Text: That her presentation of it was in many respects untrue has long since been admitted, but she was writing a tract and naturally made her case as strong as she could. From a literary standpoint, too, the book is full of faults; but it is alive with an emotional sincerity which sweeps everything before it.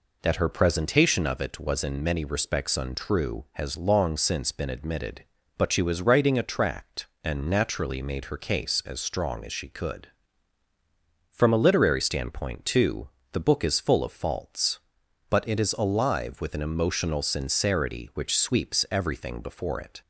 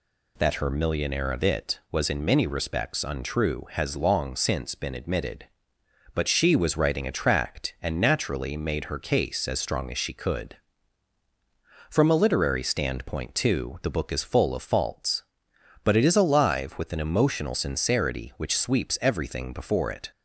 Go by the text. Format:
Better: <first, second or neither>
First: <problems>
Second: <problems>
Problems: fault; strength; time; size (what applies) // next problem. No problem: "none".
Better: first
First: none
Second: says "millionaire" for "presentation"; at 0.7 s